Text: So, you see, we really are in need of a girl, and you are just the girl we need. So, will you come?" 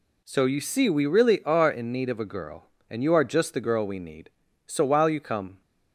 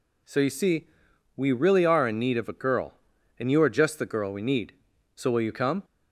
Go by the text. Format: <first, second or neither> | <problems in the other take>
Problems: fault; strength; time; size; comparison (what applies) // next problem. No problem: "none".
second | says "while" for "will"; at 4.8 s